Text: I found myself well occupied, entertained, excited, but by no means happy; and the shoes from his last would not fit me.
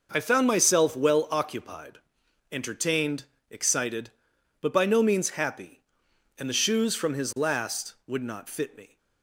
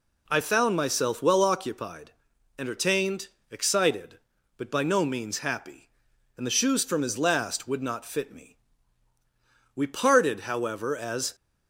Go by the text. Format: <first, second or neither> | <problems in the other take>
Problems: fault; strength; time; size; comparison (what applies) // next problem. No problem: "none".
first | goes on to say "We parted however as"; from 9.7 s on; 1.6 s long